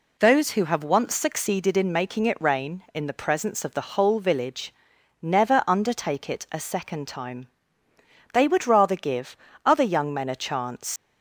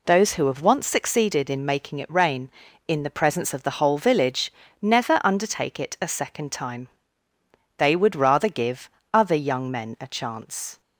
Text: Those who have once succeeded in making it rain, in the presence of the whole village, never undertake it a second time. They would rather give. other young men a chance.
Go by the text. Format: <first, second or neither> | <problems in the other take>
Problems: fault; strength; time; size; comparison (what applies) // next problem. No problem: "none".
second | leaves "chance" unfinished; at 10.9 s; 90 ms